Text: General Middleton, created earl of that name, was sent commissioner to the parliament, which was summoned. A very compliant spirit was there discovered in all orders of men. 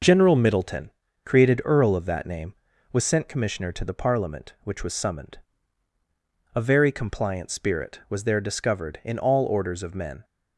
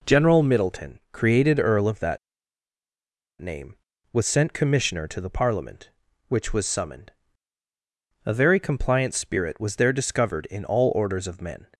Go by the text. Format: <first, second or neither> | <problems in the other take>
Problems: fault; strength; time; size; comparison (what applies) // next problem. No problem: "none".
first | pauses between "that" and "name"; at 2.1 s; 1.2 s long